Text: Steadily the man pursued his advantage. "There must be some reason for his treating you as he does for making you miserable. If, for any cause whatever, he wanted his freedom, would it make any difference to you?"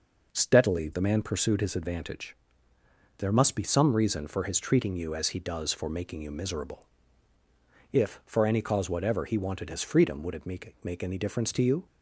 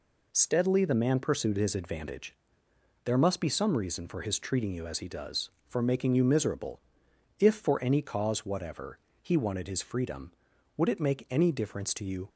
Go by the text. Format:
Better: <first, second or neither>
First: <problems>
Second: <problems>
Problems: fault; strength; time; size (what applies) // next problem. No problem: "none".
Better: second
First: says "make" twice; at 10.8 s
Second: none